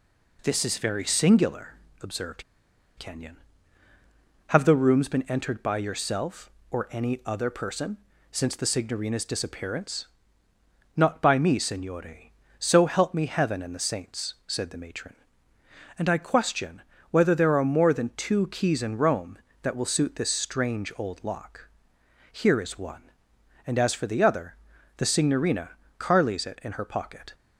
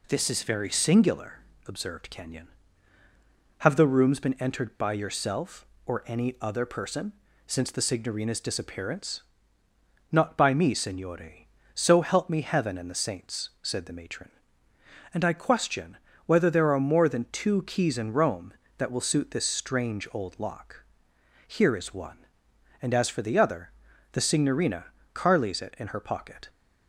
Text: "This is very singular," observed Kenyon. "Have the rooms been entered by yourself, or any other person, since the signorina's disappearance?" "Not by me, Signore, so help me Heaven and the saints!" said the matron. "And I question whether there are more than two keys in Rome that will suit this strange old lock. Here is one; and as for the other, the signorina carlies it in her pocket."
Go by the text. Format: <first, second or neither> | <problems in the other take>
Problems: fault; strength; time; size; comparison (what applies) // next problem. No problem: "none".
second | pauses between "observed" and "Kenyon"; noticeable; at 2.4 s; 0.56 s long // pauses between "question" and "whether"; slight; at 16.8 s; 0.28 s long; slight in the second // pauses between "signorina" and "carlies"; slight; at 25.7 s; 0.26 s long; slight in the second